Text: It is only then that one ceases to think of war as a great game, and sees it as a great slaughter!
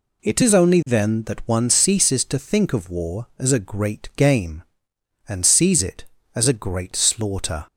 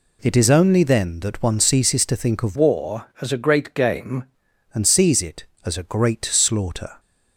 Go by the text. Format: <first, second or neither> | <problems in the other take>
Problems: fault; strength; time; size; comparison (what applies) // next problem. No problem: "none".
first | changes voice from "war" to "game"; from 2.5 to 4.2 s; 1.7 s long